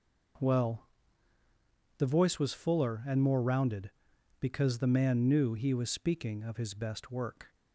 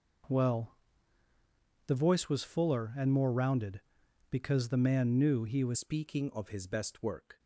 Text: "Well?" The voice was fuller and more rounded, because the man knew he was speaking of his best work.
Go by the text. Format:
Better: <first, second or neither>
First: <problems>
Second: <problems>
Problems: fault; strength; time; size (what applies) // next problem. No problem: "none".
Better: first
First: none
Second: changes voice at "speaking"; from 5.7 s on; 1.6 s long